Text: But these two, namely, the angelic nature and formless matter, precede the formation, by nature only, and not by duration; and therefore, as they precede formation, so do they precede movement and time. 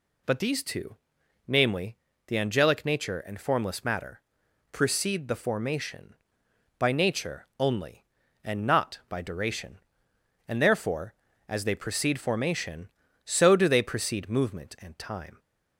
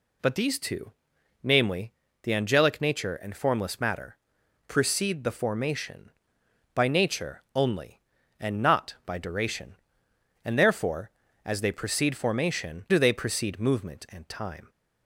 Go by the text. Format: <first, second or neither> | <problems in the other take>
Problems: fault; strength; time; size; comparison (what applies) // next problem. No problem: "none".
first | skips "so"; at 12.8 s